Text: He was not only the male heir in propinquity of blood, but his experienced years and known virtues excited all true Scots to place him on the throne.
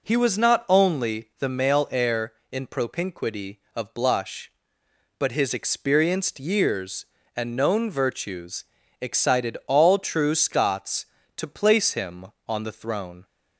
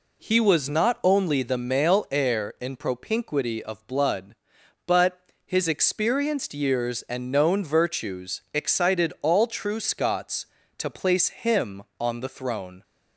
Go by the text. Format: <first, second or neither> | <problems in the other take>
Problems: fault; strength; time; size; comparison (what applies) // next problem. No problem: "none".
second | says "blush" for "blood"; at 3.9 s // pauses between "virtues" and "excited"; slight; at 8.6 s; 0.36 s long